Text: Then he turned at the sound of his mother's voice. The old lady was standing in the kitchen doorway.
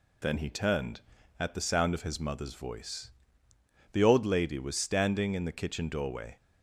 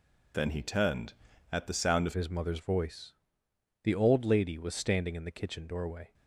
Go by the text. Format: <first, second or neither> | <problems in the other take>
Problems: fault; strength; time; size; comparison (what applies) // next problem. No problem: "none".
first | changes voice at "his"; from 2.1 s on; 4.0 s long